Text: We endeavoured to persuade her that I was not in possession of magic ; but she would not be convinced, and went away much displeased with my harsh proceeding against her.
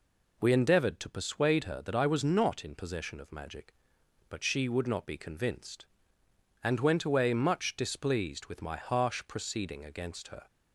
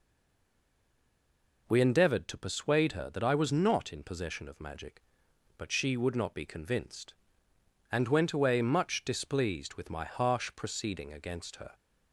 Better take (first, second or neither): first